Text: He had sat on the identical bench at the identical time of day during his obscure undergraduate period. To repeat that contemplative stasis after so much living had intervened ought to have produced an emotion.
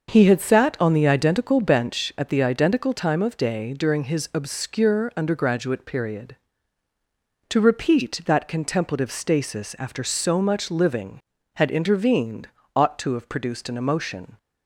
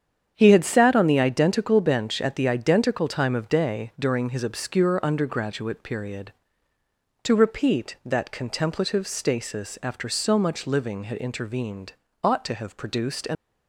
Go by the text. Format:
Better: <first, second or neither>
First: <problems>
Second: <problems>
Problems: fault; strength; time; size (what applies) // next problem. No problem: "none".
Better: first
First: starts louder than the rest; until 1.1 s; 6.5 dB // pauses between "intervened" and "ought"; slight; at 12.4 s; 0.26 s long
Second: starts louder than the rest; strong; until 1.3 s; 8 dB // pauses between "intervened" and "ought"; slight; at 11.9 s; 0.32 s long // stops before "emotion"; at 13.3 s